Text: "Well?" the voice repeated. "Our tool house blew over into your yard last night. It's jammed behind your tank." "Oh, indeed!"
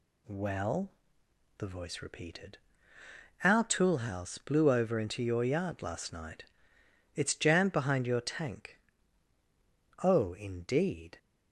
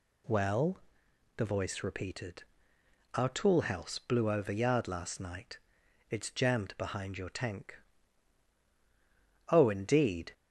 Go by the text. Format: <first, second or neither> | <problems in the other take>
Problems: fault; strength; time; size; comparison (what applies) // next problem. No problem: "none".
first | skips "into your"; at 4.5 s